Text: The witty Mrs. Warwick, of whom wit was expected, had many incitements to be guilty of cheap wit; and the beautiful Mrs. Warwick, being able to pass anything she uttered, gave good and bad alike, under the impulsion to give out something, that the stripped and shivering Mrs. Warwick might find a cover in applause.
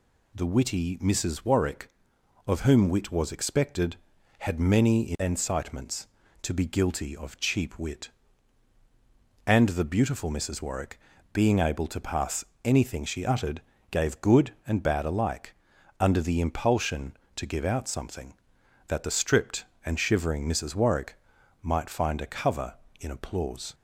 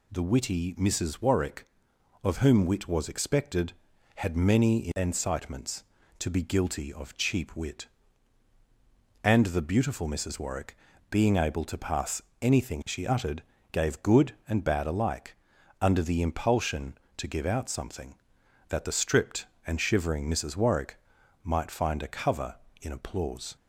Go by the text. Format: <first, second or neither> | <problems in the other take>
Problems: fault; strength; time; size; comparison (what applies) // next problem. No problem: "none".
neither | pauses between "pass" and "anything"; slight; the same in both // pauses between "Warwick" and "might"; the same in both